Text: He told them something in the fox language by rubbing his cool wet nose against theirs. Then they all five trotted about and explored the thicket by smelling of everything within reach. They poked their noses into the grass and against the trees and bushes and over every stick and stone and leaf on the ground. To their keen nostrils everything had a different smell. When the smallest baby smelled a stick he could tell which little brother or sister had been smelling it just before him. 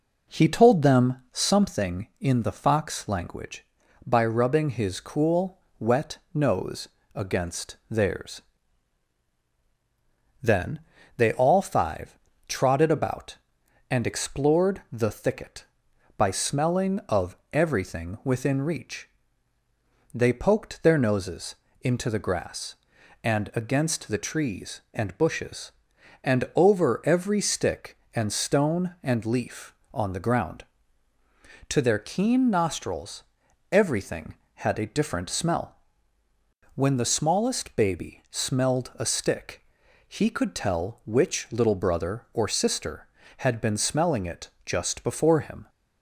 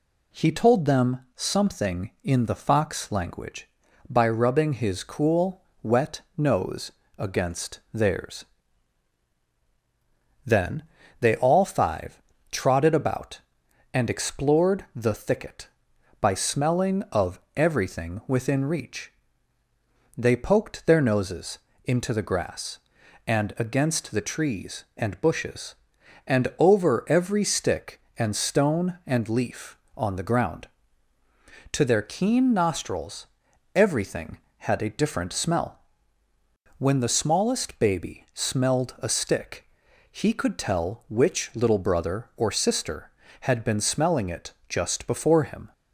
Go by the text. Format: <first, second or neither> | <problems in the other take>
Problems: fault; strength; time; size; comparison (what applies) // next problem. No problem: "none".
second | starts louder than the rest; noticeable; until 1.9 s; 4.5 dB // pauses between "them" and "something"; slight; at 1.1 s; 0.16 s long; slight in the second // pauses between "cool" and "wet"; slight; at 5.5 s; 0.20 s long; slight in the second // pauses between "wet" and "nose"; slight; at 6.1 s; 0.16 s long; slight in the second // pauses between "nose" and "against"; slight; at 6.8 s; 0.28 s long; slight in the second // pauses between "Then" and "they"; slight; at 10.8 s; 0.36 s long; slight in the second // pauses between "five" and "trotted"; slight; at 12.1 s; 0.30 s long; slight in the second // pauses between "of" and "everything"; slight; at 17.3 s; 0.16 s long; slight in the second // pauses between "noses" and "into"; slight; at 21.5 s; 0.26 s long; slight in the second // pauses between "nostrils" and "everything"; noticeable; at 33.2 s; 0.48 s long; noticeable in the second // pauses between "stick" and "he"; noticeable; at 39.6 s; 0.46 s long; noticeable in the second // pauses between "it" and "just"; slight; at 44.4 s; 0.16 s long; slight in the second